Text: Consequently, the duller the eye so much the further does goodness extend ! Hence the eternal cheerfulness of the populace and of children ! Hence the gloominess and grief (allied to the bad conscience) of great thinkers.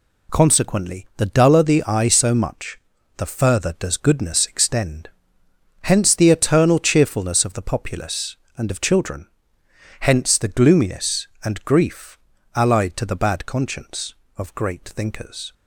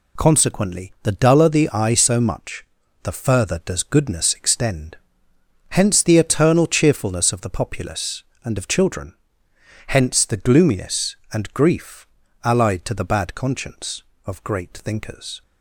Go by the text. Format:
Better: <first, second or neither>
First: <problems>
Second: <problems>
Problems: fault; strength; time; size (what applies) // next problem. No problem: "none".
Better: neither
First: pauses between "much" and "the"; at 2.7 s; 0.38 s long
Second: pauses between "much" and "the"; at 2.6 s; 0.38 s long